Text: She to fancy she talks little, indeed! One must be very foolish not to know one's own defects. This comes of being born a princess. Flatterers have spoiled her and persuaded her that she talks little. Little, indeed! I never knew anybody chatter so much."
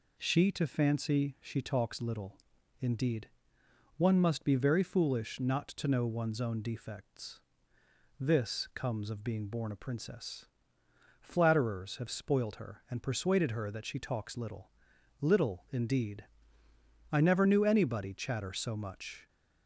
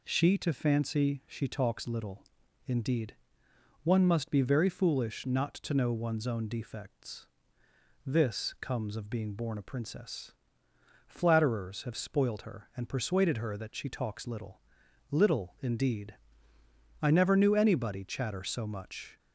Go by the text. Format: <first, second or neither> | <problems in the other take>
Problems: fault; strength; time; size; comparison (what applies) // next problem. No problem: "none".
neither | none